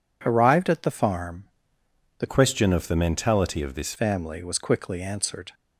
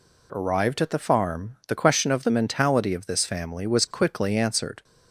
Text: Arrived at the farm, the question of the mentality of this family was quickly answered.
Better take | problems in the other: second | changes voice from "question" to "this"; from 2.2 to 3.9 s; 1.7 s long

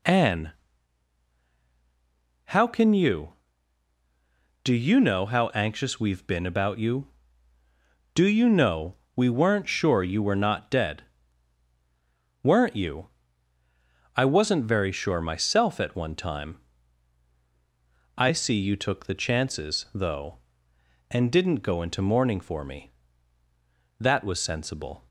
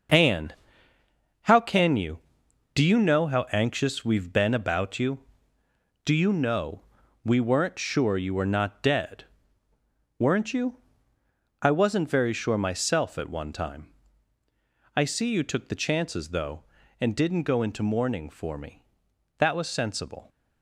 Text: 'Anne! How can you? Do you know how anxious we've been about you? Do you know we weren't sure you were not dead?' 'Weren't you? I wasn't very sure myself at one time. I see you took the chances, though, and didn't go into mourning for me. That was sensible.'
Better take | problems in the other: first | gets quieter; strong; throughout; 8.5 dB // pauses between "know" and "we"; at 6.8 s; 0.42 s long; slight in the first

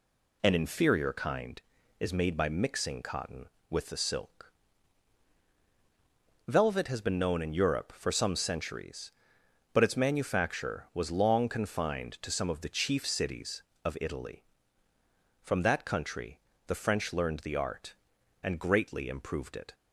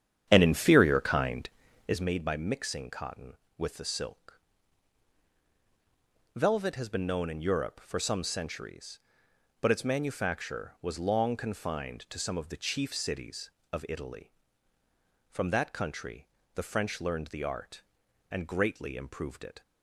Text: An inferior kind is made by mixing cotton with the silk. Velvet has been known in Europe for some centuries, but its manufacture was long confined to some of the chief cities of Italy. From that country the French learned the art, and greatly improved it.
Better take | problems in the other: first | starts louder than the rest; strong; until 2.1 s; 9.5 dB // pauses between "country" and "the"; slight; at 16.2 s; 0.28 s long; slight in the first

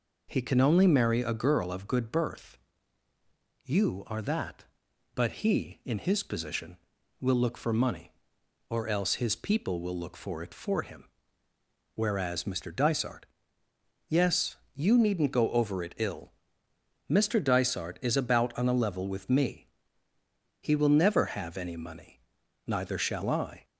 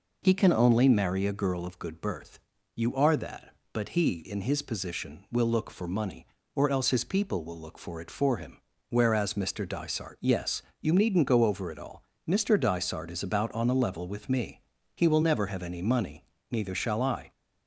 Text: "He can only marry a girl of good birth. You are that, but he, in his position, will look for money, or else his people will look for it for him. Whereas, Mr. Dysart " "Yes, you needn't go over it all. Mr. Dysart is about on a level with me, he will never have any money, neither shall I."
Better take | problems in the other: second | says "ill" for "all"; at 15.9 s

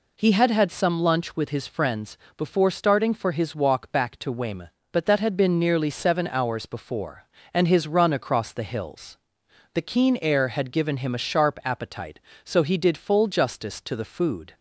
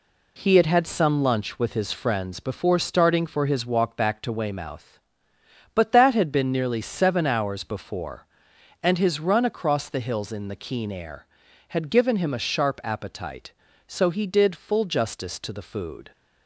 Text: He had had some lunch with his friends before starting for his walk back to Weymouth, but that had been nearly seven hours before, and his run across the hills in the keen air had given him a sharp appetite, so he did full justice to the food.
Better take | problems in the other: second | pauses between "friends" and "before"; slight; at 2.1 s; 0.22 s long // skips "in"; at 9.4 s

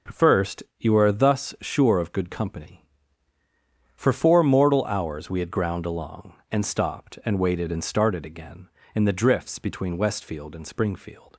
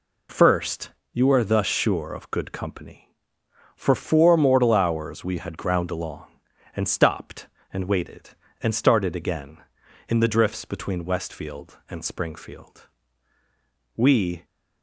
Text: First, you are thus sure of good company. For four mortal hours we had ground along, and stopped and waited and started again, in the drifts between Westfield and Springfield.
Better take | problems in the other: first | goes on to say "We"; slight; from 13.9 s on; 0.48 s long

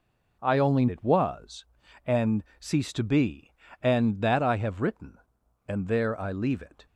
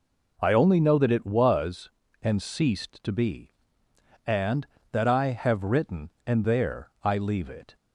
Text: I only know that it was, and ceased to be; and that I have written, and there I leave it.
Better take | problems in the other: second | skips "know that"; at 0.8 s // pauses between "and" and "ceased"; slight; at 2.4 s; 0.16 s long

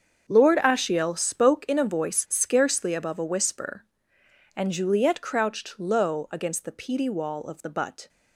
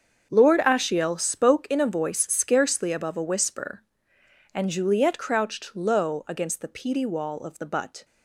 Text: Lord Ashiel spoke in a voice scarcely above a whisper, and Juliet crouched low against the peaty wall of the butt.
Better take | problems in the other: neither | starts louder than the rest; the same in both

